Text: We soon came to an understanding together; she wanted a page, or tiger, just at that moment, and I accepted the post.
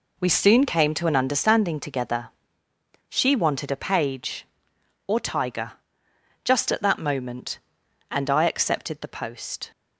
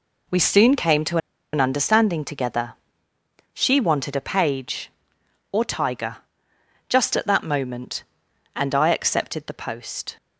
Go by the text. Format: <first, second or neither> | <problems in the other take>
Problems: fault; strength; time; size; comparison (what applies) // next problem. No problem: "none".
first | pauses between "to" and "an"; slight; at 1.1 s; 0.36 s long